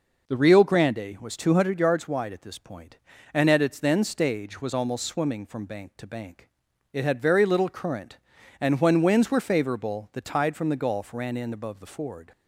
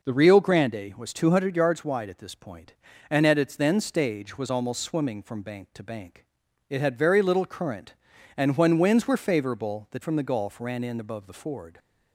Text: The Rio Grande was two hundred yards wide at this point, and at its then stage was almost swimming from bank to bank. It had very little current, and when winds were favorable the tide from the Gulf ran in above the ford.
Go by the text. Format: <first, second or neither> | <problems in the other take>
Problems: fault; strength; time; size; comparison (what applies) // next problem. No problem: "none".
first | skips "tide"; at 10.0 s